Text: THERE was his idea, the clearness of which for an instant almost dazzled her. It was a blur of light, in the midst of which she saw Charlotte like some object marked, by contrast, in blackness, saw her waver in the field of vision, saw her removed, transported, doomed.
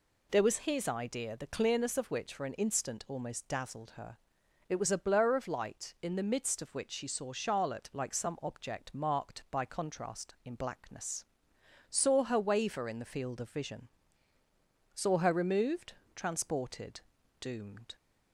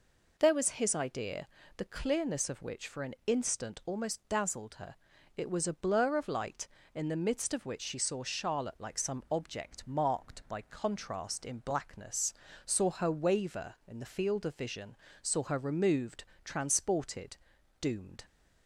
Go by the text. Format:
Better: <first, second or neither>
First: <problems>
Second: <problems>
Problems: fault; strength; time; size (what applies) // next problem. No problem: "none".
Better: neither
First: none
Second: none